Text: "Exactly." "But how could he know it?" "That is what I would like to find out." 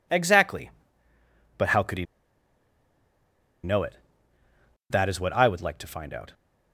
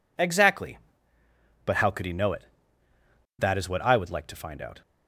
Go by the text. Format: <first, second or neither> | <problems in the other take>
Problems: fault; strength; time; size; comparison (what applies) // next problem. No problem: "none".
second | pauses between "he" and "know"; strong; at 2.0 s; 1.5 s long